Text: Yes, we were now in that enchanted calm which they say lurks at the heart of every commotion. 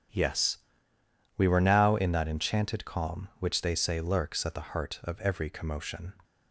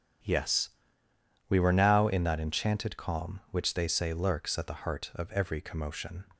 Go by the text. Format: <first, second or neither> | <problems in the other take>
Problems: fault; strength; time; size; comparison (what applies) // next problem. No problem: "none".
neither | starts louder than the rest; strong; the same in both